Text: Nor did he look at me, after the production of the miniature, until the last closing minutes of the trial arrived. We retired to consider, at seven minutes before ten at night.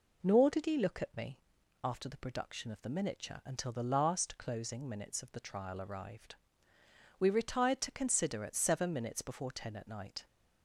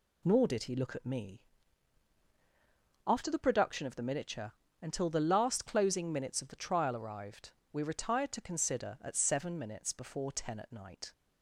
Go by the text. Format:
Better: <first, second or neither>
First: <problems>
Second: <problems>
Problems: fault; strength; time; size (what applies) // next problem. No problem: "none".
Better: neither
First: none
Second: none